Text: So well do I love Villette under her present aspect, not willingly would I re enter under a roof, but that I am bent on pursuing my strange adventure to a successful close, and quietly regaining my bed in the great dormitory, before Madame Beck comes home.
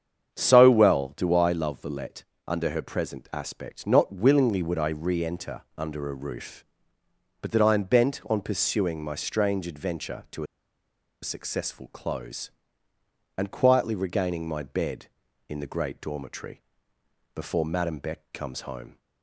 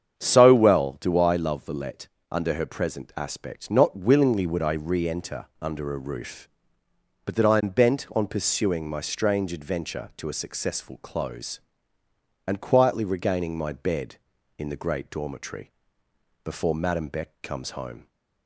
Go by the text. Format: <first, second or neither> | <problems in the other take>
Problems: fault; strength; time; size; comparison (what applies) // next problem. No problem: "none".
second | starts louder than the rest; strong; until 1.3 s; 7.5 dB; strong in the second // pauses between "Villette" and "under"; slight; at 2.2 s; 0.22 s long; slight in the second // pauses between "enter" and "under"; slight; at 5.6 s; 0.16 s long; slight in the second // pauses between "a" and "successful"; noticeable; at 10.4 s; 0.78 s long